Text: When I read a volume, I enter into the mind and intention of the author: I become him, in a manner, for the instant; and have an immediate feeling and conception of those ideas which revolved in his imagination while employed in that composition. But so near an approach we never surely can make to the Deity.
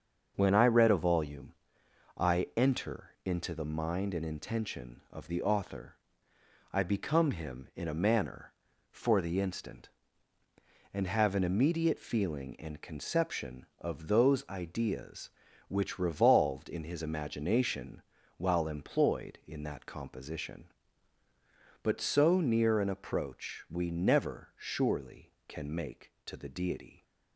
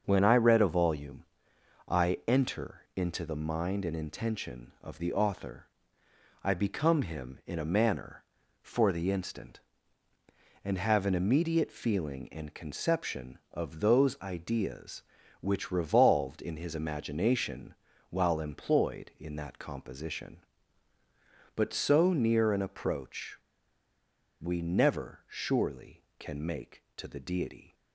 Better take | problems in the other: first | starts louder than the rest; until 1.0 s; 6.5 dB; also in the first // pauses between "imagination" and "while"; at 17.7 s; 0.38 s long; also in the first // pauses between "approach" and "we"; at 23.3 s; 1.0 s long

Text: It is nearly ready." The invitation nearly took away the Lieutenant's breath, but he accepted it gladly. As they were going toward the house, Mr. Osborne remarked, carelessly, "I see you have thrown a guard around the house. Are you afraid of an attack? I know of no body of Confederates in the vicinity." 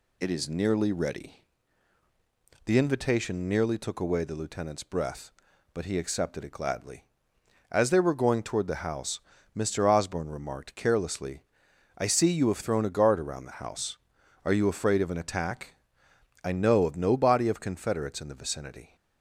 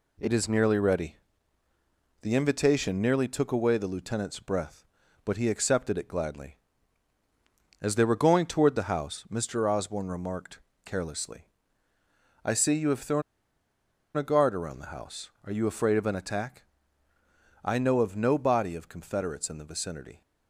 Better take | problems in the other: first | pauses between "thrown" and "a"; noticeable; at 13.2 s; 0.94 s long

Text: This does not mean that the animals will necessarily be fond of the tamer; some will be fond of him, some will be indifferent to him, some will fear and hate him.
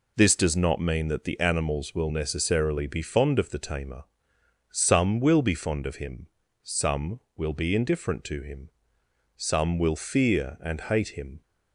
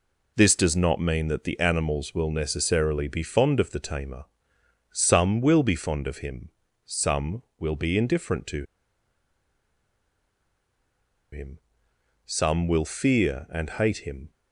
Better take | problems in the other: first | pauses between "to" and "him"; strong; at 8.6 s; 2.6 s long

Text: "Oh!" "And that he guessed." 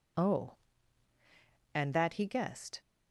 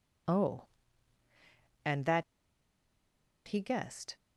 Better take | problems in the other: first | pauses between "that" and "he"; at 2.2 s; 1.2 s long

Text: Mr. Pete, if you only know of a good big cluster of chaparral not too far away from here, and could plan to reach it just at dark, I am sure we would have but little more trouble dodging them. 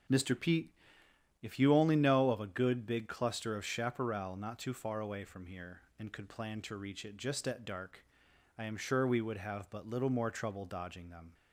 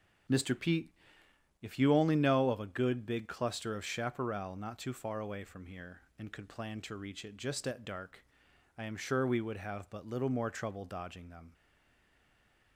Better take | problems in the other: first | starts louder than the rest; strong; until 2.0 s; 7 dB; also in the first // stays silent after the last word; noticeable; from 11.5 s on; 1.2 s long

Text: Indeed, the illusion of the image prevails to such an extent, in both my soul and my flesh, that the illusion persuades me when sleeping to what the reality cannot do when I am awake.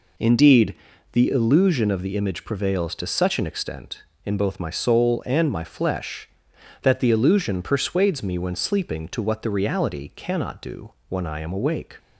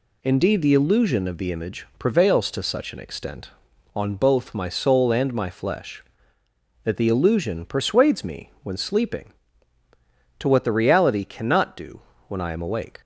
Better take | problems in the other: first | says "on" for "in"; at 3.9 s // pauses between "do" and "when"; slight; at 12.0 s; 0.28 s long; slight in the first

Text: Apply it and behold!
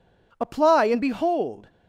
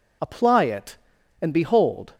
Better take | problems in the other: second | skips "it"; at 0.9 s

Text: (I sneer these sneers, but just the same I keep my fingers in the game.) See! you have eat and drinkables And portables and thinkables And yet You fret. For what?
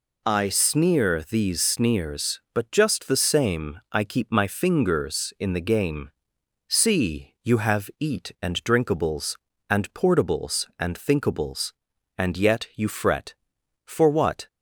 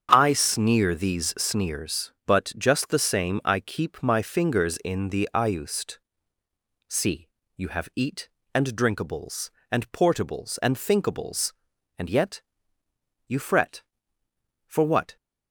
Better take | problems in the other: first | starts louder than the rest; strong; until 1.1 s; 7.5 dB // says "iust" for "game"; at 5.3 s // pauses between "yet" and "You"; noticeable; at 12.4 s; 0.86 s long

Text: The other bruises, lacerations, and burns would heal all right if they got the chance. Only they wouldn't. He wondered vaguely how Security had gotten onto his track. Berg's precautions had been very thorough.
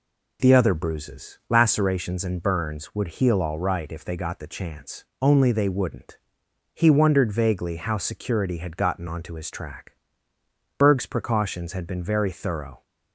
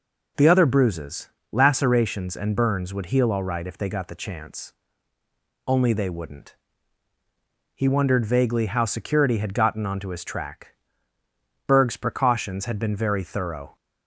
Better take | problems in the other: neither | none

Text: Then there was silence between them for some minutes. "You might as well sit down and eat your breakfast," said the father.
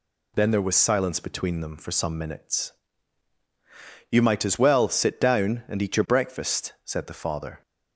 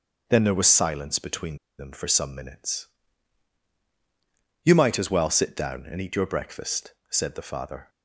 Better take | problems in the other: first | starts louder than the rest; until 1.2 s; 6.5 dB // pauses between "between" and "them"; slight; at 1.5 s; 0.22 s long

